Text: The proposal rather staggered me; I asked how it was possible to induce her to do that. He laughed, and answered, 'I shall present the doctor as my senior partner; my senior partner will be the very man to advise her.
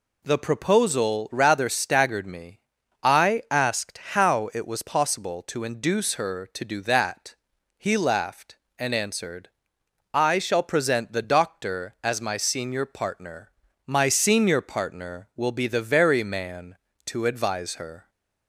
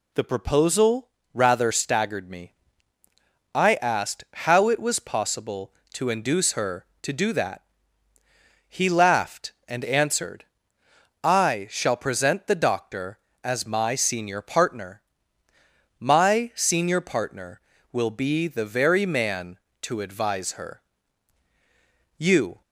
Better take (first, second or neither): first